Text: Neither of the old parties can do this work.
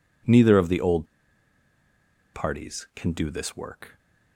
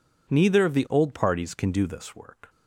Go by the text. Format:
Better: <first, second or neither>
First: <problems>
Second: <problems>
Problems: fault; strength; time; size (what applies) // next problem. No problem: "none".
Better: second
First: pauses between "old" and "parties"; strong; at 1.0 s; 1.2 s long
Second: none